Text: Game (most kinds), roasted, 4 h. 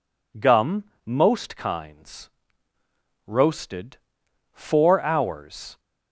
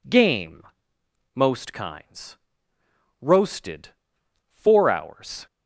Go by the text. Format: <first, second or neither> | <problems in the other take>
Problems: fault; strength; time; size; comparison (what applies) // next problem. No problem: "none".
second | says "Gum" for "Game"; at 0.3 s